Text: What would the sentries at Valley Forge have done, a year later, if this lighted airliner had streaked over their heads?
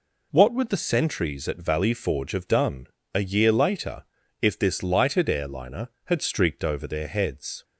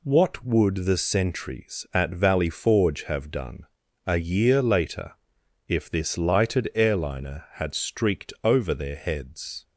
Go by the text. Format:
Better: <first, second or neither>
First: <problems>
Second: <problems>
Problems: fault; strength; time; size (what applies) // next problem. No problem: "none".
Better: neither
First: none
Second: none